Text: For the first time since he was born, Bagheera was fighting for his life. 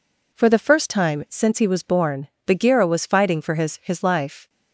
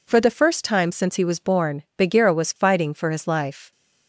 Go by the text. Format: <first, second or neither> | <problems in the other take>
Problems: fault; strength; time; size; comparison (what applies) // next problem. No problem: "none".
second | says "his" twice; at 3.8 s